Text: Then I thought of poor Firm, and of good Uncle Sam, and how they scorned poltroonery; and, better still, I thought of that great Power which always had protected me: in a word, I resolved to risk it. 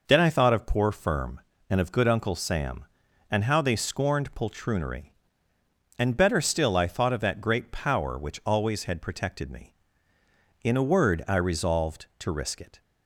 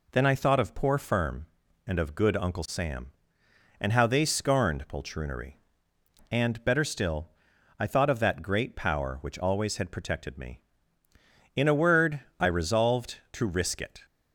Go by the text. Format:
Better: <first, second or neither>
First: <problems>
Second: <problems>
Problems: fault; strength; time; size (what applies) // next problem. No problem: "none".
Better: neither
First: none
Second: none